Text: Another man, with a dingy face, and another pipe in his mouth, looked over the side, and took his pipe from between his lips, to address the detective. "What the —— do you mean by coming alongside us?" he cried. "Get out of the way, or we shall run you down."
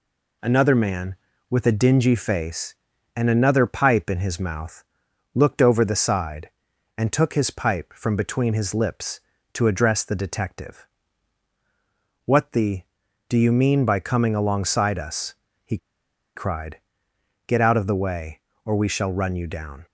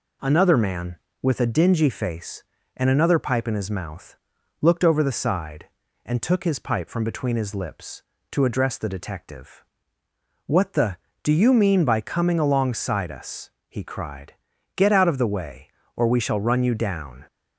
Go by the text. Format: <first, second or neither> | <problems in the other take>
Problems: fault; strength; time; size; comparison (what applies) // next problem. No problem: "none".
second | pauses between "he" and "cried"; noticeable; at 15.7 s; 0.58 s long